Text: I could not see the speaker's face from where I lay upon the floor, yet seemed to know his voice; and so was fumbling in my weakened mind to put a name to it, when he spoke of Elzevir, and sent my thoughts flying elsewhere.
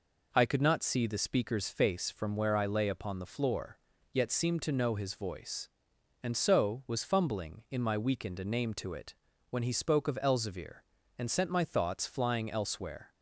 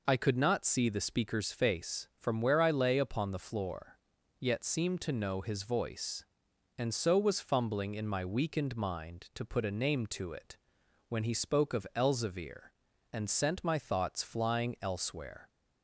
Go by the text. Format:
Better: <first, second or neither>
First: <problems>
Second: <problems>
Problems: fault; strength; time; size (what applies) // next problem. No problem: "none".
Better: second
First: skips "mind to put"; at 8.3 s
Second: none